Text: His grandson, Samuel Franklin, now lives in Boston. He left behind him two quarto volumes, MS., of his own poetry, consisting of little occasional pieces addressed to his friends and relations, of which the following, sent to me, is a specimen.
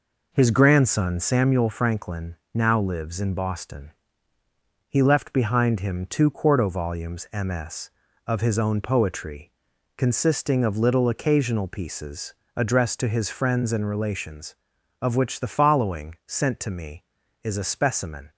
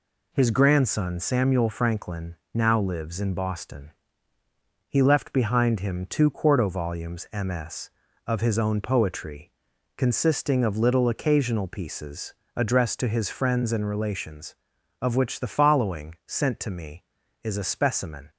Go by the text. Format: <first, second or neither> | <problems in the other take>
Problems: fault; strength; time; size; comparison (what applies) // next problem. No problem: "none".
second | starts louder than the rest; noticeable; until 1.6 s; 4.5 dB // pauses between "pieces" and "addressed"; slight; at 12.3 s; 0.24 s long; slight in the second